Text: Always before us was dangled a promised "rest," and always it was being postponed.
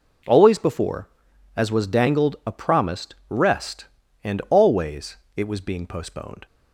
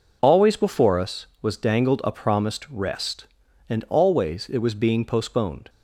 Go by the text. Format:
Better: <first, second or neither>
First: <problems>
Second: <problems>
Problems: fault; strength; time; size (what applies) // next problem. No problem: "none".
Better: second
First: says "as" for "us"; at 1.5 s // pauses between "promised" and "rest"; slight; at 3.1 s; 0.16 s long // pauses between "always" and "it"; slight; at 5.1 s; 0.18 s long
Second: none